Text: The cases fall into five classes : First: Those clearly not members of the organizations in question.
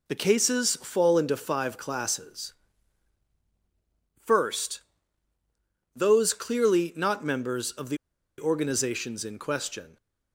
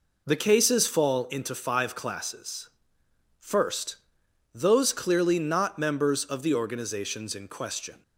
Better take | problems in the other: second | pauses between "the" and "organizations"; at 7.9 s; 0.41 s long

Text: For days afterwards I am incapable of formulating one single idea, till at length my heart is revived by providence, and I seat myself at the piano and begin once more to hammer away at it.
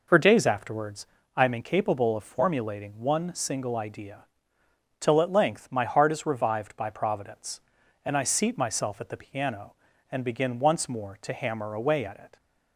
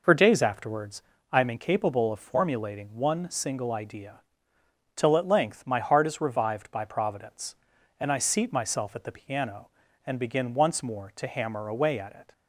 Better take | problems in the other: neither | pauses between "afterwards" and "I"; slight; the same in both

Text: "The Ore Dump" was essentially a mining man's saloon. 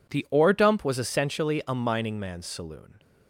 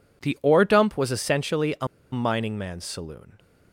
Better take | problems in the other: first | pauses between "a" and "mining"; slight; at 1.8 s; 0.24 s long

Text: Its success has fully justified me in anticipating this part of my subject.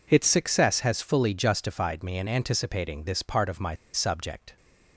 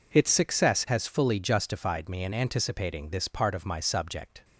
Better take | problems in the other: second | pauses between "my" and "subject"; slight; at 3.7 s; 0.18 s long

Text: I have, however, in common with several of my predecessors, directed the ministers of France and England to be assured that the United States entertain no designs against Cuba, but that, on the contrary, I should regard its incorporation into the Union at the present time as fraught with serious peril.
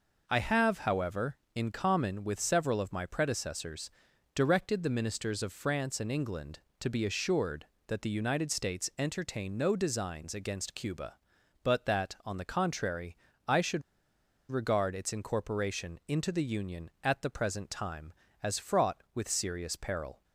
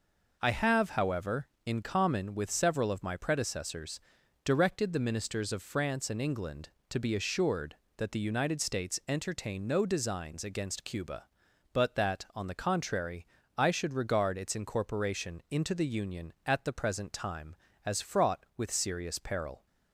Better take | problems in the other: second | pauses between "should" and "regard"; noticeable; at 13.8 s; 0.69 s long

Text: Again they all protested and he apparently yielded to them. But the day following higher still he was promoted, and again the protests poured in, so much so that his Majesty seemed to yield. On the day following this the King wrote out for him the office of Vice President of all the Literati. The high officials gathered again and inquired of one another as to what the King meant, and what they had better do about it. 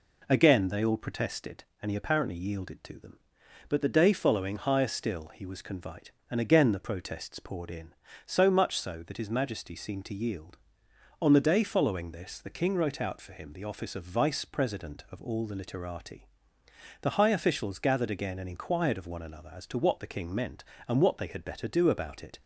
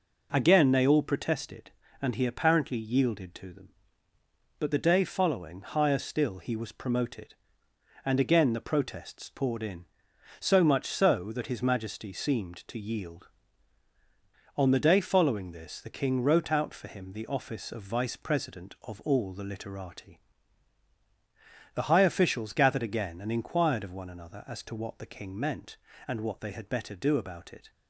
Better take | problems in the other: second | says "convite" for "promoted"; at 5.6 s

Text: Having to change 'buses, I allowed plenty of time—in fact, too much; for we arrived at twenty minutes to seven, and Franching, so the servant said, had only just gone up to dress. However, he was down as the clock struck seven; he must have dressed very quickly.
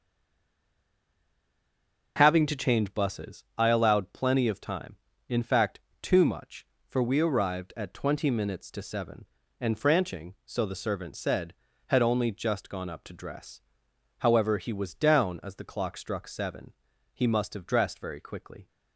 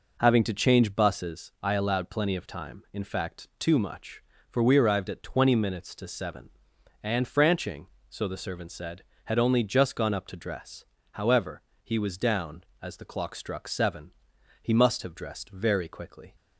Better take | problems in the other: second | stays silent before the first word; until 2.1 s; 2.1 s long // starts louder than the rest; until 3.1 s; 6 dB

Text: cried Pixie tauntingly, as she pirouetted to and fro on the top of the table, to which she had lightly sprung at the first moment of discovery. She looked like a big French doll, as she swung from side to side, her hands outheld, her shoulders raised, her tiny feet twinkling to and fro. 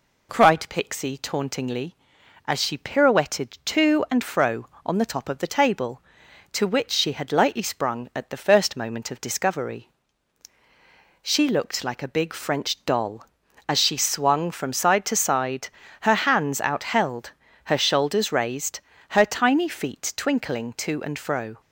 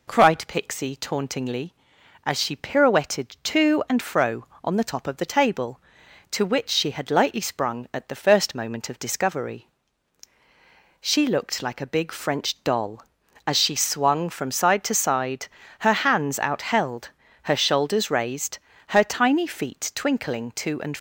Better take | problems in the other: first | stops before "fro"; at 20.9 s

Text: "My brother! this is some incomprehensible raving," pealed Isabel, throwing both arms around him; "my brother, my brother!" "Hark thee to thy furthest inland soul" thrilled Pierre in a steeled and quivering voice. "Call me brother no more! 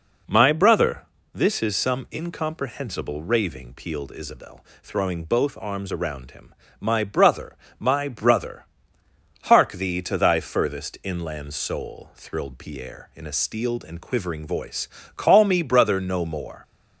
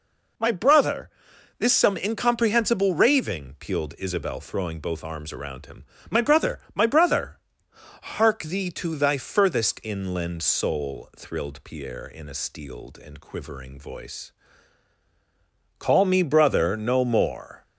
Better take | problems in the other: first | skips "is"; at 1.7 s

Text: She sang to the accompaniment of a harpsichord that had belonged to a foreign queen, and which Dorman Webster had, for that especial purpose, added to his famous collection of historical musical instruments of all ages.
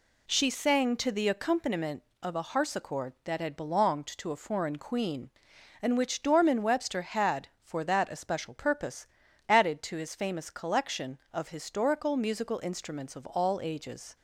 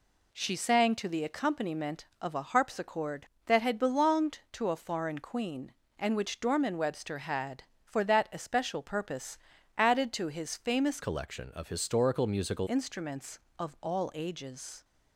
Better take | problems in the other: first | changes voice from "collection" to "musical"; from 11.0 to 12.6 s; 1.6 s long

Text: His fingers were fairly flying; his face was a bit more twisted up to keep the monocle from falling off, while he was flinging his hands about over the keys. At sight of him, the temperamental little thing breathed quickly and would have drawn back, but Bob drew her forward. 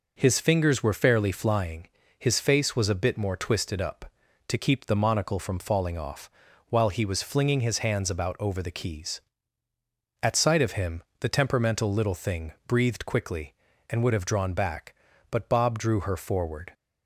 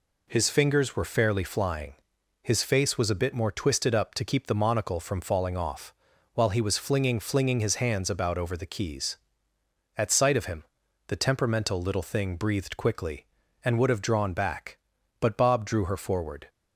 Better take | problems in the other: first | says "flinging" twice; at 7.1 s

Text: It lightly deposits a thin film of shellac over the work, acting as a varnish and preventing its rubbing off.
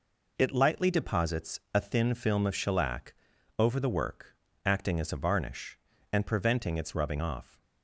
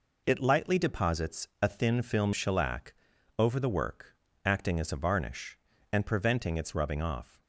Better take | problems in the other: first | skips "of"; at 2.3 s // pauses between "shellac" and "over"; at 2.9 s; 0.44 s long; also in the first

